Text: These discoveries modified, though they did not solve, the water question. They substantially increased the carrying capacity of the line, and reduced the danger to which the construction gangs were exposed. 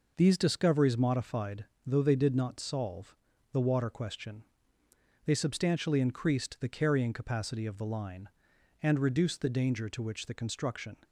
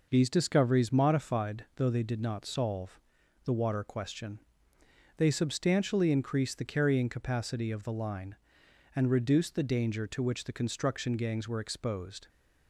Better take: second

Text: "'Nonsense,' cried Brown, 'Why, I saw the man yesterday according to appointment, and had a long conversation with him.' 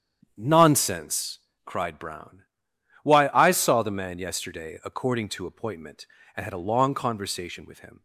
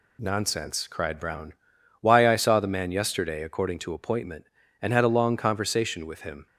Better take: second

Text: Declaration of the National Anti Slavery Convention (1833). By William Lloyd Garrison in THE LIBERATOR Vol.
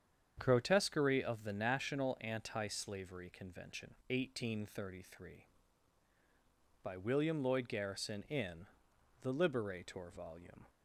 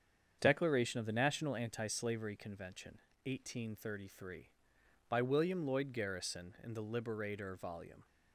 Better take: second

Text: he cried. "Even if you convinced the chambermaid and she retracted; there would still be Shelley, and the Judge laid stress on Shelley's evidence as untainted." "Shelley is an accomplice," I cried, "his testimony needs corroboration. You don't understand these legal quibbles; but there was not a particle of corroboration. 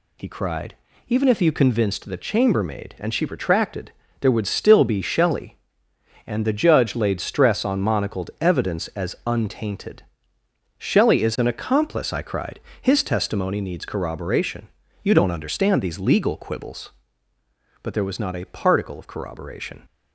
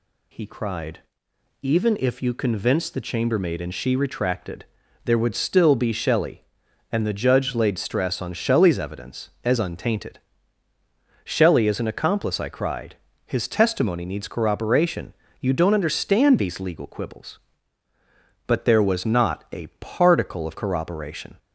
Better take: second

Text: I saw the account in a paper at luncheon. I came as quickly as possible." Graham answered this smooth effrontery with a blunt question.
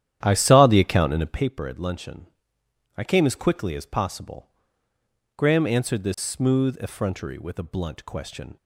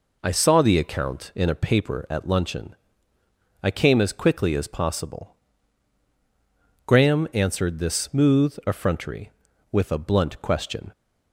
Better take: second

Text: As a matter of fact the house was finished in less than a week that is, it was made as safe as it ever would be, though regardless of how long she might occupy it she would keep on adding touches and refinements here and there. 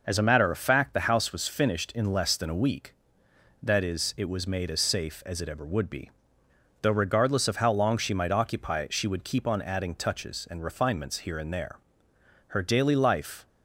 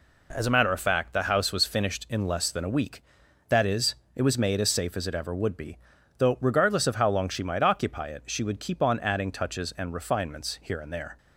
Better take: second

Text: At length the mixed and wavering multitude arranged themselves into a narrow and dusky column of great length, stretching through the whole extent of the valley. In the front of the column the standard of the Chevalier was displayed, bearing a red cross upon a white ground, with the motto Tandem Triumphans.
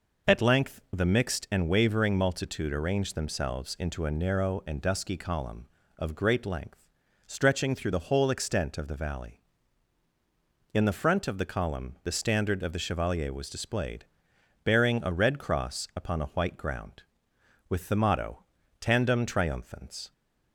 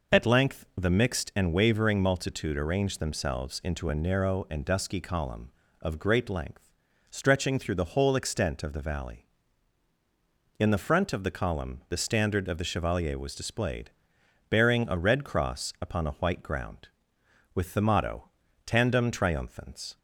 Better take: neither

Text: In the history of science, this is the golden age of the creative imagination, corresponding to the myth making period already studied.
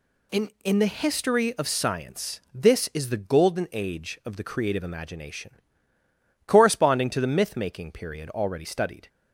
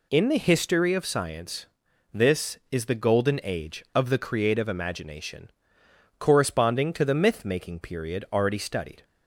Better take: second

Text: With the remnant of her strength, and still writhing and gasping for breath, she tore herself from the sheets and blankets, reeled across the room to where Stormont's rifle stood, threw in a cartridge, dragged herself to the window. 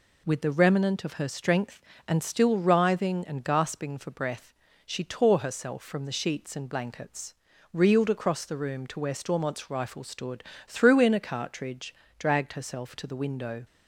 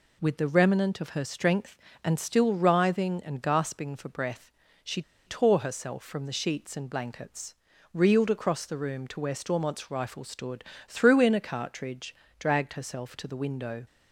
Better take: first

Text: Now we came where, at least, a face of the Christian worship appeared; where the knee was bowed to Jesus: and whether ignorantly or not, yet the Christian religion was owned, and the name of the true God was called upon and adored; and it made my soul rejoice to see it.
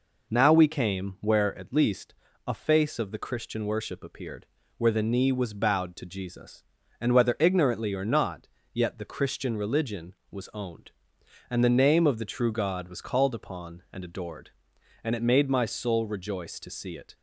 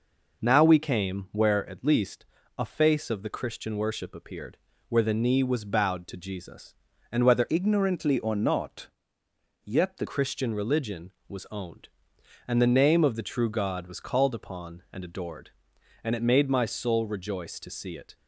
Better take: first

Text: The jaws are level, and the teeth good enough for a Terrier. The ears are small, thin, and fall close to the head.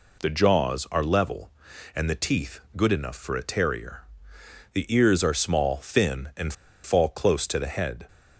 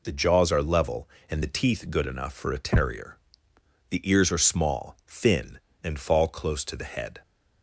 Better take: second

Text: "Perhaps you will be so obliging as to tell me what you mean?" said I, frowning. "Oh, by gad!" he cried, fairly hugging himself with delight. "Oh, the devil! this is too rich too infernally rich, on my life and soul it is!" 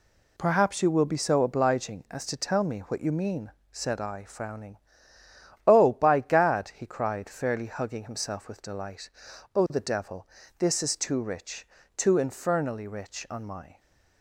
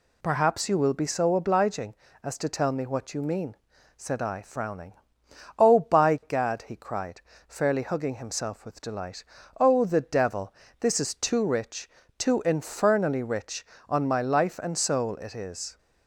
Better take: second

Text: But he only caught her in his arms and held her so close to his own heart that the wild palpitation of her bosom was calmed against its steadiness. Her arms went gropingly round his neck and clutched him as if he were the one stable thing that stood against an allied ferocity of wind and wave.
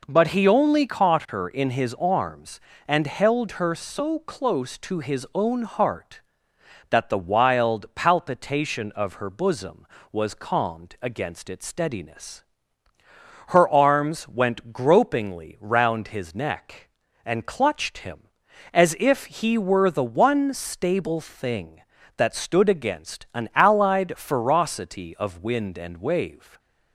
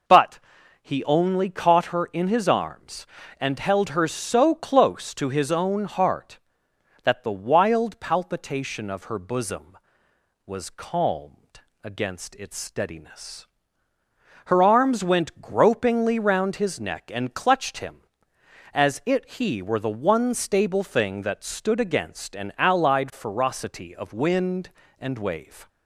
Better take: first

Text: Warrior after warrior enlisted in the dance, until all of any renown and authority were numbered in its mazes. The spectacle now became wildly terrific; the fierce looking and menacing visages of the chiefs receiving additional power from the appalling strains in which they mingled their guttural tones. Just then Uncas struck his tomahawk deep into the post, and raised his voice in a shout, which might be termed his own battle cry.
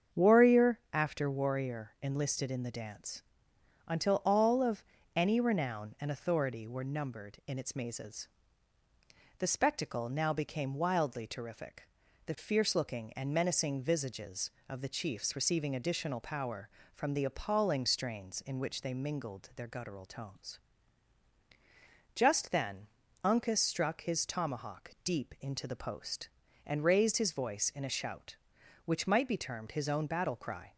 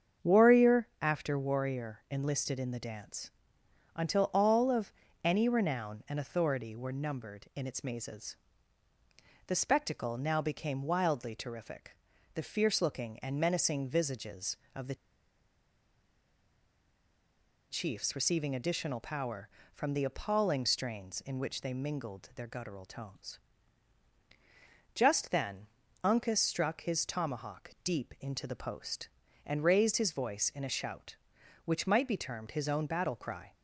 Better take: first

